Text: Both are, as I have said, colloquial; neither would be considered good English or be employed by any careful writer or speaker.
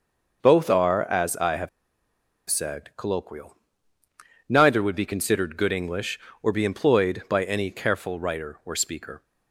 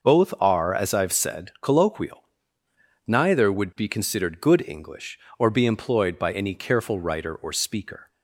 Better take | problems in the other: second | pauses between "have" and "said"; noticeable; at 1.6 s; 0.80 s long

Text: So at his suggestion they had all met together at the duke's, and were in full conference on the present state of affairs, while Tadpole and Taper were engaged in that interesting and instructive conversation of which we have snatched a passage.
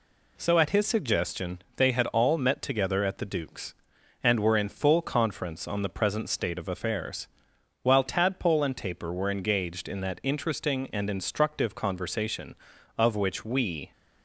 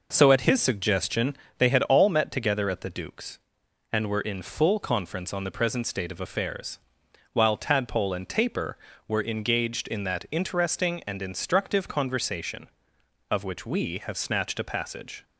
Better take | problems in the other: second | pauses between "suggestion" and "they"; slight; at 1.5 s; 0.18 s long; slight in the second // stops before "have snatched a passage"; at 13.9 s

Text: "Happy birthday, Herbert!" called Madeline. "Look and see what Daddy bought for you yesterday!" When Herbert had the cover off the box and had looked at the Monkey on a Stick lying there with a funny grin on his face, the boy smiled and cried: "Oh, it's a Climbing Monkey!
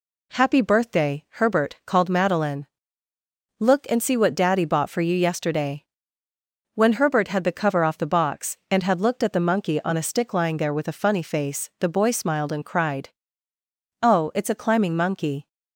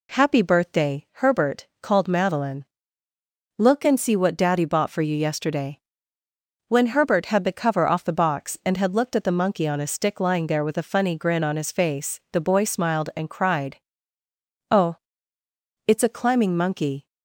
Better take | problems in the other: second | skips "grin on his"; at 11.2 s

